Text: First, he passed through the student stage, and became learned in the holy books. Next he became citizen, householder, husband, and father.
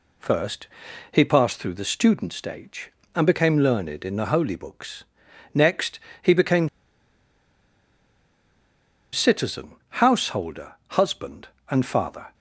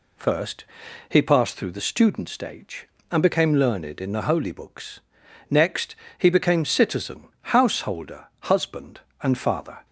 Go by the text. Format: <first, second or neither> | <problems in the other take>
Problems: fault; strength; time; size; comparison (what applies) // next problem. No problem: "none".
second | pauses between "Next" and "he"; slight; at 5.9 s; 0.24 s long; slight in the second // pauses between "became" and "citizen"; strong; at 6.6 s; 2.4 s long